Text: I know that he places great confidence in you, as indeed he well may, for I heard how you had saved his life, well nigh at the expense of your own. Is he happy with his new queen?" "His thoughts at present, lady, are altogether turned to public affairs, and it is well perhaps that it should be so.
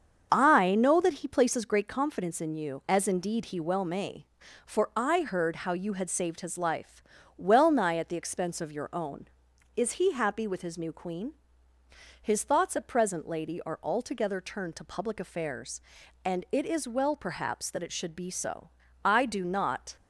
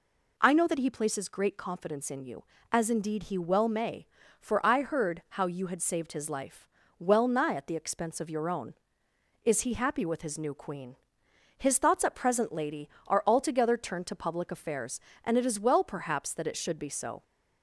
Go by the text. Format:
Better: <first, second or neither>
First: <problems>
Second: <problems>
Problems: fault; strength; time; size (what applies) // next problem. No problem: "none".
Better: second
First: starts louder than the rest; until 1.3 s; 7 dB // goes on to say "I do not"; noticeable; from 19.0 s on; 0.92 s long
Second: none